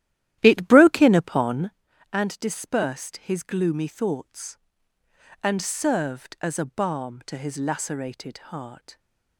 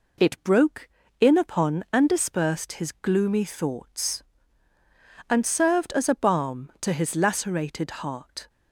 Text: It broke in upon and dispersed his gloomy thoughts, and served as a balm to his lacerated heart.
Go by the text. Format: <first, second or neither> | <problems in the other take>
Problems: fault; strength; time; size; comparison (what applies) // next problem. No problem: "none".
second | starts louder than the rest; strong; until 1.8 s; 13 dB